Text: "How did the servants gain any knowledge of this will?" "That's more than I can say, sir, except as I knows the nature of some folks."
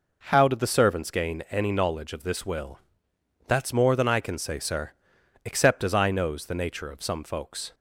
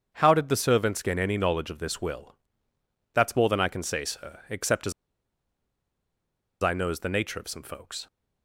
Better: first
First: none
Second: starts louder than the rest; strong; until 1.1 s; 7 dB // pauses between "as" and "I"; strong; at 4.9 s; 1.7 s long

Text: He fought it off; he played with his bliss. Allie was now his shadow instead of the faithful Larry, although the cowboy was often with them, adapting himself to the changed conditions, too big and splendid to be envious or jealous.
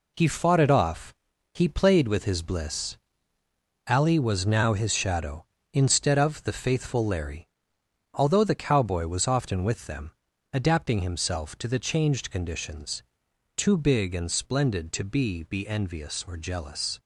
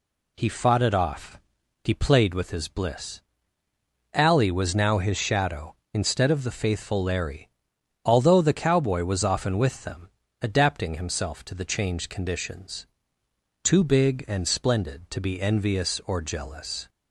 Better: second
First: says "be" twice; at 15.4 s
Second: none

